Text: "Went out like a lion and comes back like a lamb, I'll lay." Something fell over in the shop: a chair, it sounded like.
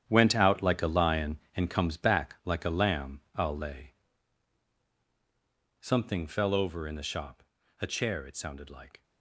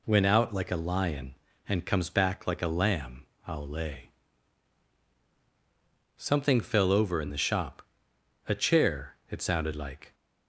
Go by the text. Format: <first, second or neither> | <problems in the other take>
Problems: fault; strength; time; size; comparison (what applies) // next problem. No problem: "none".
second | gets quieter; strong; throughout; 11.5 dB